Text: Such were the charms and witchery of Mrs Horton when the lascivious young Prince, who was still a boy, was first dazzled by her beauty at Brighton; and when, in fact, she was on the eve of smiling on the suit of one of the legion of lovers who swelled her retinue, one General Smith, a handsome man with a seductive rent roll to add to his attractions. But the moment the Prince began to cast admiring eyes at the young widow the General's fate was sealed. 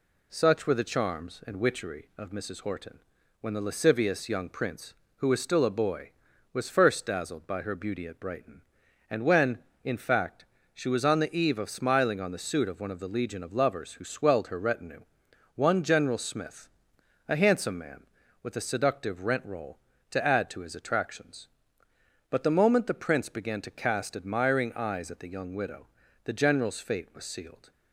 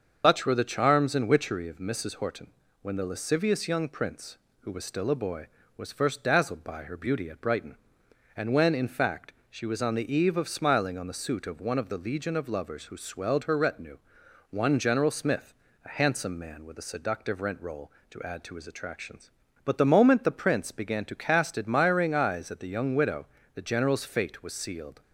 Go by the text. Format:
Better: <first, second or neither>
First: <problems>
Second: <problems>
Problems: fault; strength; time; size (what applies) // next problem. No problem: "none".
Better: first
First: pauses between "Horton" and "when"; at 2.9 s; 0.42 s long // pauses between "widow" and "the"; slight; at 25.8 s; 0.36 s long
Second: loses the start of "Such"; at 0.2 s; 150 ms // starts louder than the rest; until 1.2 s; 7 dB // pauses between "Horton" and "when"; slight; at 2.4 s; 0.32 s long // pauses between "widow" and "the"; slight; at 23.2 s; 0.30 s long